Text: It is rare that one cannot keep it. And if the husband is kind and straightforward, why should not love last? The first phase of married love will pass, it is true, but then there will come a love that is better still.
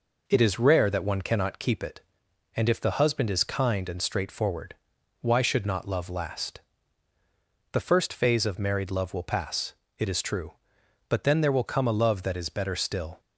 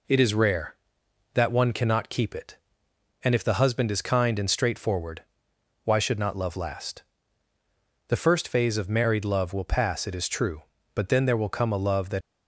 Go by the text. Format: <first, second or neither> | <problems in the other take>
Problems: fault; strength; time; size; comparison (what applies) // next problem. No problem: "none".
first | stops before "is better still"; at 12.2 s